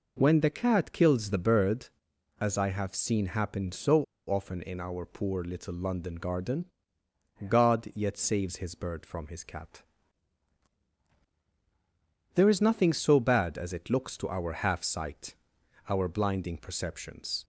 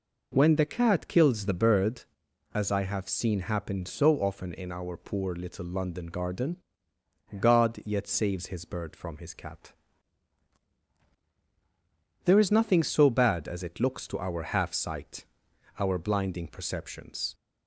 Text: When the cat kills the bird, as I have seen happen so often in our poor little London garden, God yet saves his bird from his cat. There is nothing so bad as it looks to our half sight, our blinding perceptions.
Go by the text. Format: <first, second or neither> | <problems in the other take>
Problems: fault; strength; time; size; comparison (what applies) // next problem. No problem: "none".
second | pauses between "so" and "often"; slight; at 4.0 s; 0.25 s long